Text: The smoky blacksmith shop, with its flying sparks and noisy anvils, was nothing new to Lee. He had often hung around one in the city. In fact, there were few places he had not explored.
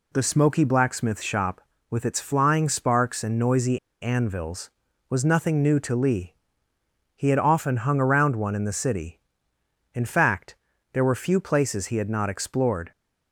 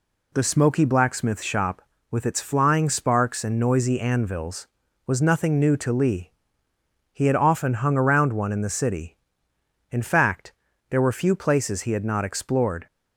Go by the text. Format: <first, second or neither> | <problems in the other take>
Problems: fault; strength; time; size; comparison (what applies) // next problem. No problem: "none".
second | pauses between "noisy" and "anvils"; slight; at 3.7 s; 0.24 s long